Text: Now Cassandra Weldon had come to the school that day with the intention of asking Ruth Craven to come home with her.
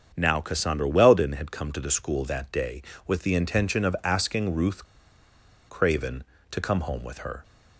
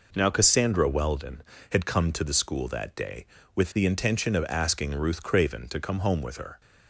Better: second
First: starts louder than the rest; strong; until 1.1 s; 7.5 dB // pauses between "Ruth" and "Craven"; noticeable; at 4.8 s; 0.84 s long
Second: none

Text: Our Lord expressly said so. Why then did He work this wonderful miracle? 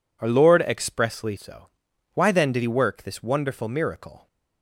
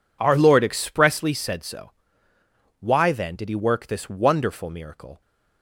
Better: second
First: skips "said"; at 1.3 s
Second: none

